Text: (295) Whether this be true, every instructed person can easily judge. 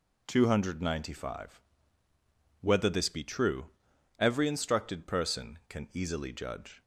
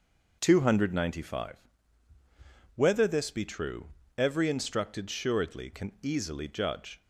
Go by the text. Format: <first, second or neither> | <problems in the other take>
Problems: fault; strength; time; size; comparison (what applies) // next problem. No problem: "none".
first | says "suredly" for "person"; at 5.0 s